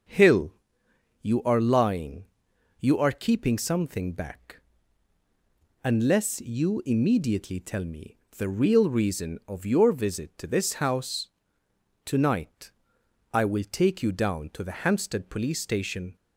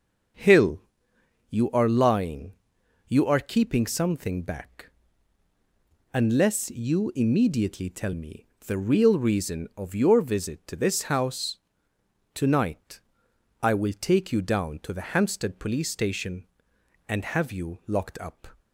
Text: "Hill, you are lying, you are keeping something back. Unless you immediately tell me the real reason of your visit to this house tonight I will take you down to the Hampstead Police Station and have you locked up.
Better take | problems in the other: second | pauses between "me" and "the"; slight; at 8.1 s; 0.22 s long; slight in the second // pauses between "house" and "tonight"; noticeable; at 11.2 s; 0.78 s long; noticeable in the second // pauses between "tonight" and "I"; noticeable; at 12.6 s; 0.64 s long; noticeable in the second // stops before "and have you locked up"; at 16.1 s

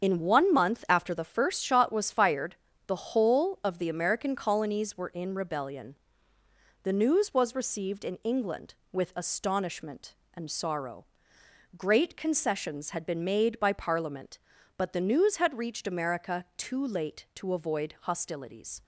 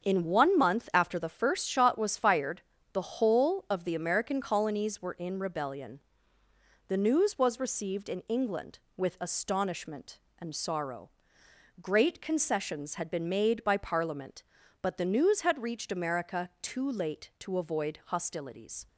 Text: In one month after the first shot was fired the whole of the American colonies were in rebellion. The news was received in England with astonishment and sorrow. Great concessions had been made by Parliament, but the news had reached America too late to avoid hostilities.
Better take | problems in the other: second | loses the start of "In"; at 0.0 s; 35 ms // starts louder than the rest; strong; until 1.0 s; 7.5 dB; strong in the second // pauses between "fired" and "the"; slight; at 2.5 s; 0.32 s long; slight in the second

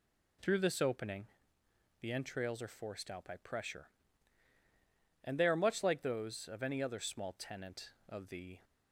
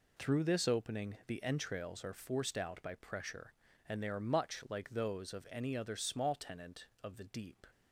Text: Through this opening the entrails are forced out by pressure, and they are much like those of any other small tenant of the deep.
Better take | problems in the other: second | pauses between "opening" and "the"; noticeable; at 1.2 s; 0.76 s long // stops before "deep"; at 8.6 s

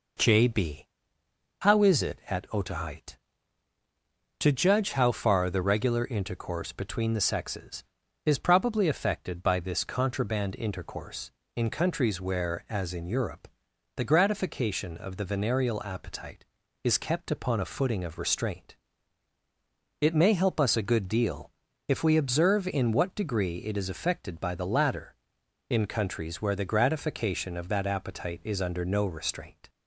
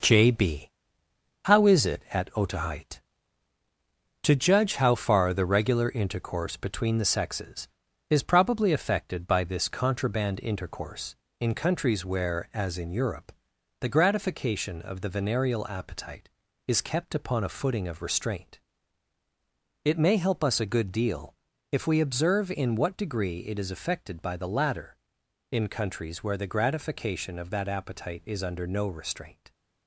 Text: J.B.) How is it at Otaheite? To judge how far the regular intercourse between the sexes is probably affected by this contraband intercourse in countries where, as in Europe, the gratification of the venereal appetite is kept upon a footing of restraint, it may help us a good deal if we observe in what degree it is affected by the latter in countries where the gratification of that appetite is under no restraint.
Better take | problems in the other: first | gets quieter; noticeable; throughout; 6 dB // pauses between "deal" and "if"; slight; at 21.3 s; 0.36 s long; slight in the first

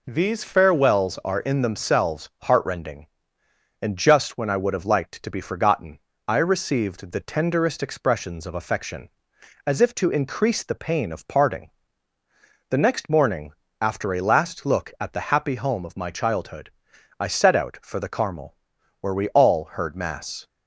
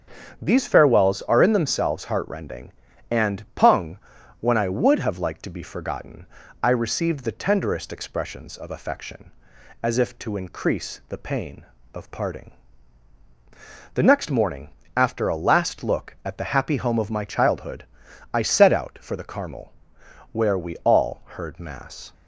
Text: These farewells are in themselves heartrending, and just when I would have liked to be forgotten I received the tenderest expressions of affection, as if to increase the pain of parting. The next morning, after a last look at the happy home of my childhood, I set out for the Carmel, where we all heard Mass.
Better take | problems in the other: first | starts louder than the rest; strong; until 1.4 s; 8 dB // says "pung" for "just"; at 3.5 s // pauses between "forgotten" and "I"; at 6.2 s; 0.38 s long; slight in the first

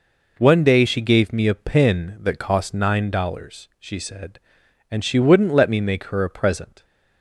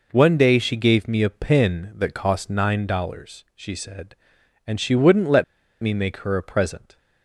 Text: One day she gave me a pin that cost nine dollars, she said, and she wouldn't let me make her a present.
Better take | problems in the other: first | pauses between "let" and "me"; at 5.4 s; 0.38 s long

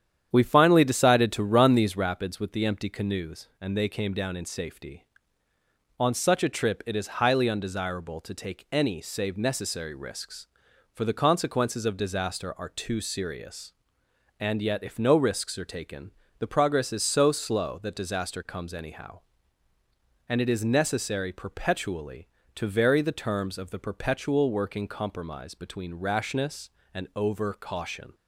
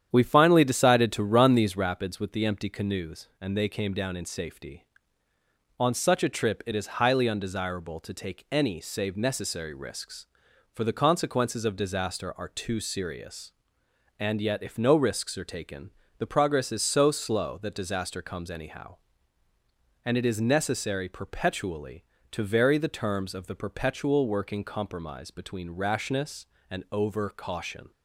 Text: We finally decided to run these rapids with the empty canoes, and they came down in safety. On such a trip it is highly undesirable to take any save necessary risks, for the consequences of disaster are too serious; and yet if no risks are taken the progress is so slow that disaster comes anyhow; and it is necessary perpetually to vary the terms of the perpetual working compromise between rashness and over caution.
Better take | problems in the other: neither | starts louder than the rest; strong; the same in both // pauses between "taken" and "the"; slight; the same in both

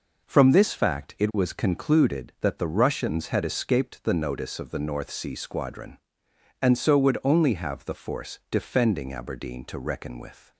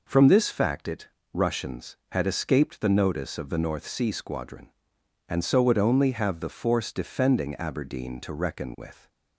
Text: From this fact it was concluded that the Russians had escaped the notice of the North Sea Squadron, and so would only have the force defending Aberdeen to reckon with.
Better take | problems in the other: first | skips "was concluded that the"; at 1.2 s

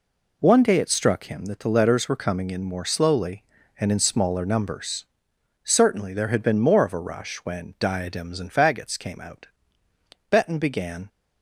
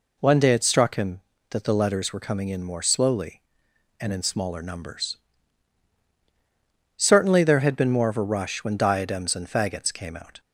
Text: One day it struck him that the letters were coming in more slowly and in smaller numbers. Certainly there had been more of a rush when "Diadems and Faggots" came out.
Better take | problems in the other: second | goes on to say "Betton began"; noticeable; from 10.3 s on; 0.78 s long

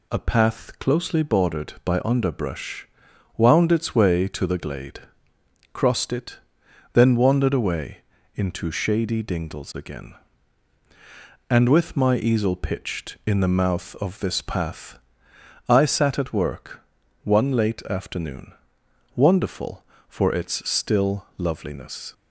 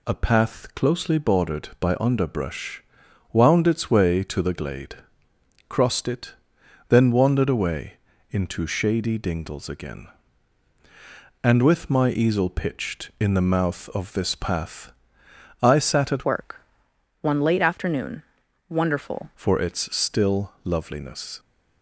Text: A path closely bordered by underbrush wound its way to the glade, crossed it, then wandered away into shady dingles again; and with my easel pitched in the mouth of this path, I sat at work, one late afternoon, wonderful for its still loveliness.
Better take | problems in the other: first | pauses between "underbrush" and "wound"; noticeable; at 2.8 s; 0.52 s long; noticeable in the first // pauses between "away" and "into"; slight; at 7.9 s; 0.34 s long; slight in the first // changes voice from "work" to "wonderful"; from 16.2 to 19.3 s; 3.1 s long

